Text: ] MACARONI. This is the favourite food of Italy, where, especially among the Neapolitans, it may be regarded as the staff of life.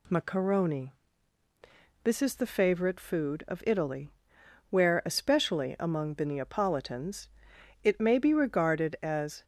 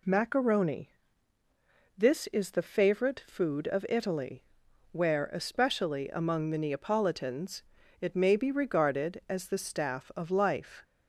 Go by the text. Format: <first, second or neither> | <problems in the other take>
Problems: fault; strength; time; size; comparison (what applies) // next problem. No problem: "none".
second | stops before "the staff of life"; at 9.4 s